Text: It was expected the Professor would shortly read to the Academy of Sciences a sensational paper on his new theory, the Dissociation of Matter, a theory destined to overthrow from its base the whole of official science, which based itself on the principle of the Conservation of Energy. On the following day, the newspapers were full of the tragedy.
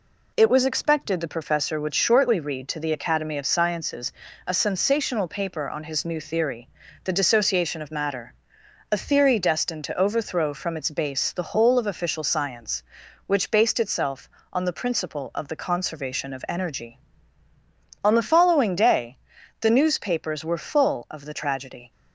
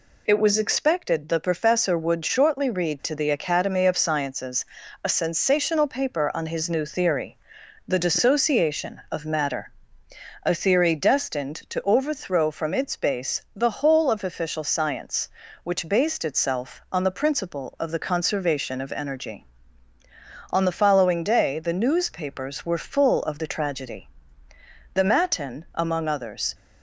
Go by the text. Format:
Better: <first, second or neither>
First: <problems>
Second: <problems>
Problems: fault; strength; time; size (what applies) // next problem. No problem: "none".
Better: first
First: pauses between "Sciences" and "a"; slight; at 4.1 s; 0.34 s long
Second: pauses between "Sciences" and "a"; at 4.6 s; 0.40 s long // goes on to say "The Matin among others"; from 24.9 s on; 1.6 s long